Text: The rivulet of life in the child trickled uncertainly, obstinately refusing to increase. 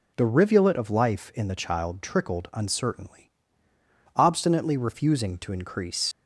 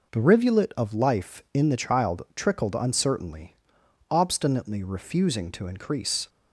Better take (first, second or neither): second